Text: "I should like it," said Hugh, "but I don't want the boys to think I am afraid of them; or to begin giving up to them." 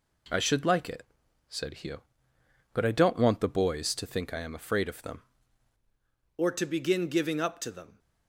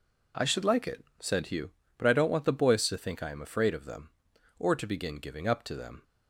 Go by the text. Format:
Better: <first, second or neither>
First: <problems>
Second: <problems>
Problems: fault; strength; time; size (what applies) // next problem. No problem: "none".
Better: second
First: changes voice at "or"; from 6.3 s on; 1.6 s long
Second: none